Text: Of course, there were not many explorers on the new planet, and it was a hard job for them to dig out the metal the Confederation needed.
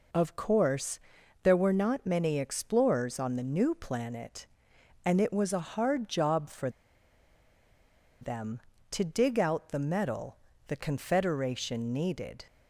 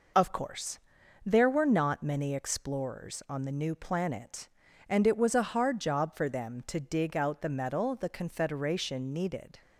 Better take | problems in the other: second | pauses between "for" and "them"; strong; at 6.6 s; 1.5 s long // pauses between "metal" and "the"; slight; at 10.3 s; 0.32 s long

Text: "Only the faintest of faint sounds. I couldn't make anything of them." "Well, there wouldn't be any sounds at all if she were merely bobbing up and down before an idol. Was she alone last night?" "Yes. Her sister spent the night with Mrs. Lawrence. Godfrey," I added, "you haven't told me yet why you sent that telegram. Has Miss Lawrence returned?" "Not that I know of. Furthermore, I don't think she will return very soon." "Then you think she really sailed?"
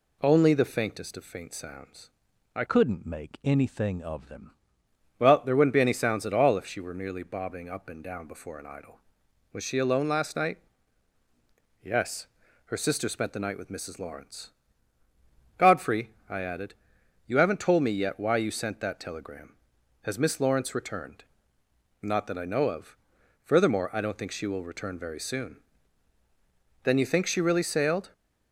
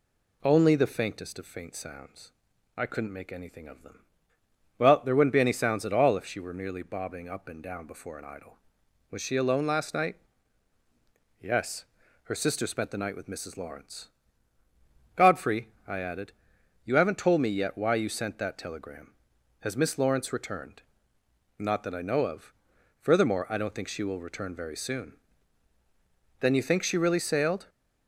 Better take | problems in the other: second | changes voice from "couldn't" to "them"; from 2.6 to 4.5 s; 1.9 s long

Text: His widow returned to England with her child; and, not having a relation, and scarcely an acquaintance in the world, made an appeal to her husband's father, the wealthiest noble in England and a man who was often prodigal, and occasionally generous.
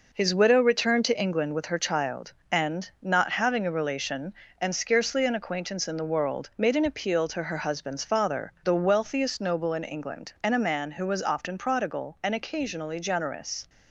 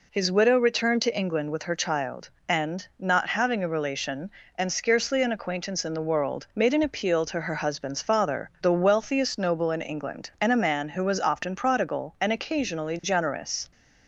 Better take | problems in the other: second | gets quieter; throughout; 6.5 dB

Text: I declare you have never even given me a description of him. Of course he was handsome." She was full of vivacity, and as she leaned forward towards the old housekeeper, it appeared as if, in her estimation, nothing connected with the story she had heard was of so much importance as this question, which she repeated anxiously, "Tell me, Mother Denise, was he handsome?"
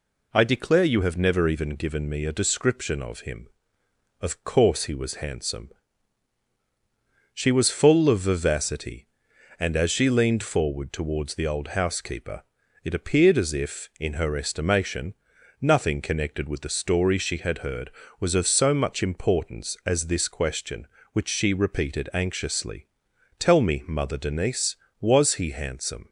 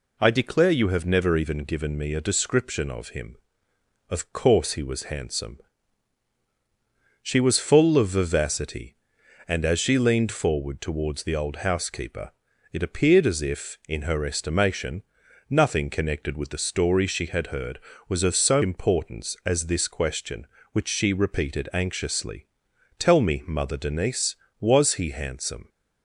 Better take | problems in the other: first | skips "much"; at 18.6 s

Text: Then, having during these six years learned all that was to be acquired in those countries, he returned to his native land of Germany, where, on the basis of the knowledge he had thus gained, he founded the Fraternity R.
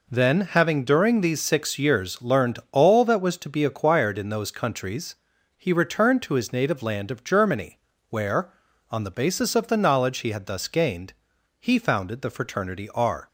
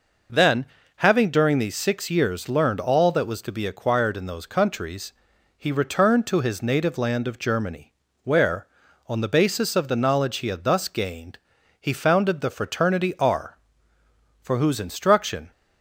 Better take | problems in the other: first | goes on to say "for whose instruction"; noticeable; from 14.4 s on; 1.1 s long

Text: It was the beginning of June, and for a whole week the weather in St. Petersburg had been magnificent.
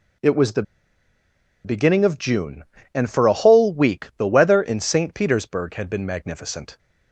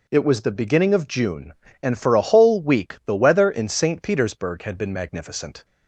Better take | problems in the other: second | pauses between "the" and "beginning"; at 0.6 s; 1.0 s long

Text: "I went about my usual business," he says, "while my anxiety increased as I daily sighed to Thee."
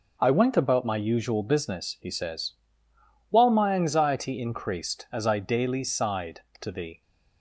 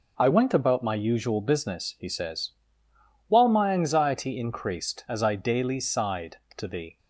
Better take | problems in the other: neither | none

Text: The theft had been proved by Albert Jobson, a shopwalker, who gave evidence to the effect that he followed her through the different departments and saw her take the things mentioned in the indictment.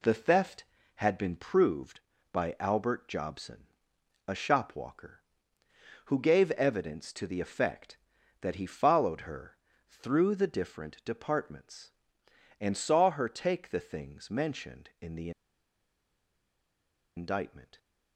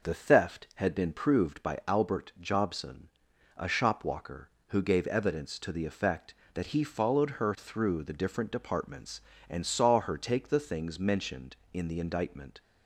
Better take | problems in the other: second | pauses between "her" and "through"; slight; at 9.5 s; 0.32 s long // pauses between "the" and "indictment"; strong; at 15.3 s; 1.8 s long

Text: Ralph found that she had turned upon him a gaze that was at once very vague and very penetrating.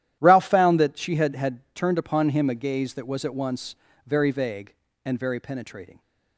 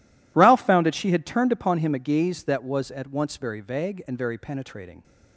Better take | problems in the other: second | starts louder than the rest; strong; until 1.2 s; 12 dB // says "had" twice; at 1.3 s // pauses between "once" and "very"; slight; at 3.7 s; 0.30 s long

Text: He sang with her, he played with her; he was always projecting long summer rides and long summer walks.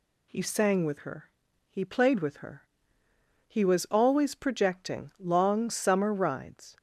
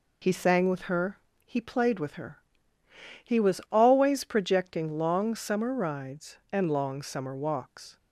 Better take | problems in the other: second | stops before "and long summer walks"; at 6.7 s

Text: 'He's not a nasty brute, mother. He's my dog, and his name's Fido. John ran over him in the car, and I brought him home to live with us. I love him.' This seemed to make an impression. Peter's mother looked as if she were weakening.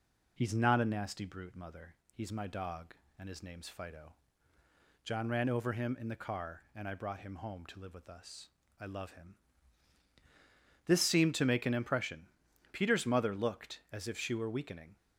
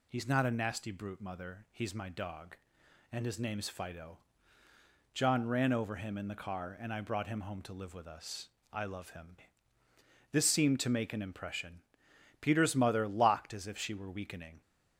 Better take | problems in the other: first | says "locked" for "looked"; at 13.0 s

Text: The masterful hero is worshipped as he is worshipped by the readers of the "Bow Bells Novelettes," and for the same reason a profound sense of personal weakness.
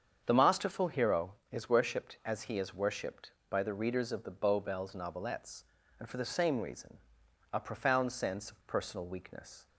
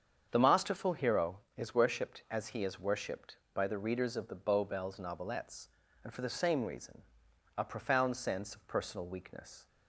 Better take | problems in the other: neither | starts louder than the rest; strong; the same in both // pauses between "reason" and "a"; noticeable; the same in both

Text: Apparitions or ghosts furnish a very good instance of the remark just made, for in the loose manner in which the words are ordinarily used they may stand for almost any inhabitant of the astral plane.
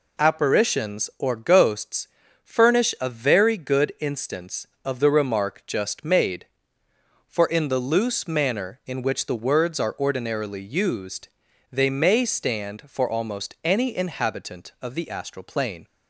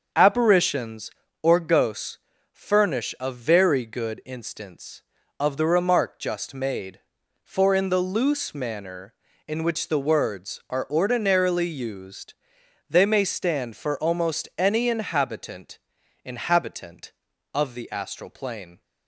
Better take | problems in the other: first | starts louder than the rest; until 1.4 s; 6.5 dB // pauses between "ghosts" and "furnish"; slight; at 2.1 s; 0.34 s long; slight in the first // pauses between "used" and "they"; noticeable; at 12.3 s; 0.56 s long; also in the first // says "inhabitant" twice; at 16.2 s

